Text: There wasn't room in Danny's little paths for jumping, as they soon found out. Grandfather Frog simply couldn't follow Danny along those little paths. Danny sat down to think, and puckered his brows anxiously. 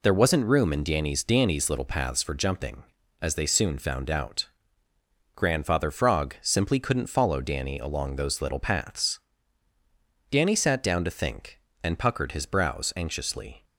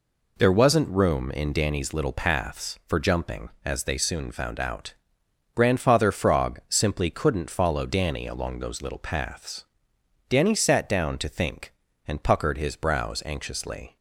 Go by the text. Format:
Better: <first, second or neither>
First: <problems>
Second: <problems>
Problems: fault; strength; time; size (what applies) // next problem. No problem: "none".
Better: second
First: says "Danny's" twice; at 1.2 s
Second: none